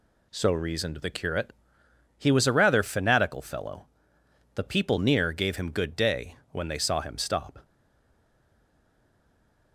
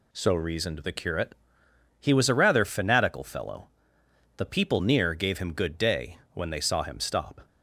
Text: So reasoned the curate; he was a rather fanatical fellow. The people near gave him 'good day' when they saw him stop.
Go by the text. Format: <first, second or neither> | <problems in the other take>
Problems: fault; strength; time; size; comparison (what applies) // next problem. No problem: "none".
second | pauses between "day" and "when"; slight; at 6.3 s; 0.16 s long; slight in the second // stays silent after the last word; from 7.6 s on; 2.1 s long